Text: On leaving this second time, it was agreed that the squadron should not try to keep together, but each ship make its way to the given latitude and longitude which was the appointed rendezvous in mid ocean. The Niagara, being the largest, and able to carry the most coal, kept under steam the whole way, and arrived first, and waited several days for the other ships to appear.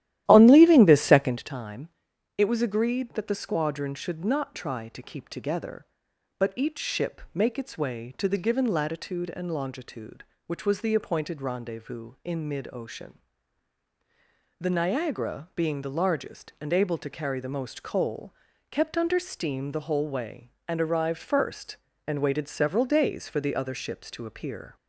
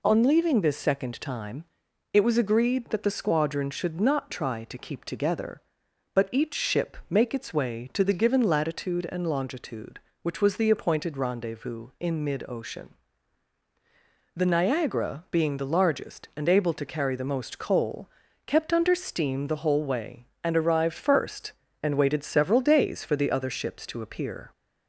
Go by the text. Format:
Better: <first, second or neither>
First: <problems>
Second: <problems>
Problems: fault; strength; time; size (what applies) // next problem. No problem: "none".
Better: second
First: starts louder than the rest; strong; until 1.5 s; 13.5 dB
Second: none